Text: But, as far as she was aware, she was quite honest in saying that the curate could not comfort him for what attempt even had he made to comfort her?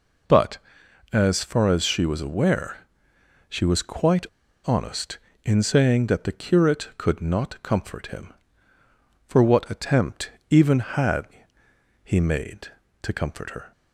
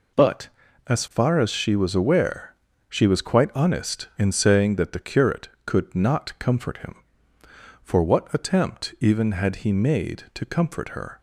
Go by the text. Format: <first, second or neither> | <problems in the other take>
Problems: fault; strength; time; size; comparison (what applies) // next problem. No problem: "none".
second | pauses between "quite" and "honest"; at 4.2 s; 0.40 s long // pauses between "attempt" and "even"; slight; at 10.3 s; 0.18 s long // pauses between "had" and "he"; noticeable; at 11.2 s; 0.78 s long